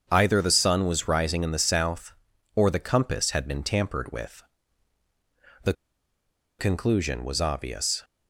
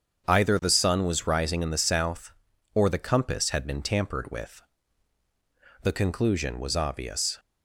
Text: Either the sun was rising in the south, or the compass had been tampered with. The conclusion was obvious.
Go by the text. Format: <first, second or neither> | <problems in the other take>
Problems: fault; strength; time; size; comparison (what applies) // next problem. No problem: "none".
second | starts louder than the rest; strong; until 1.1 s; 7 dB; strong in the second // pauses between "The" and "conclusion"; noticeable; at 5.7 s; 0.86 s long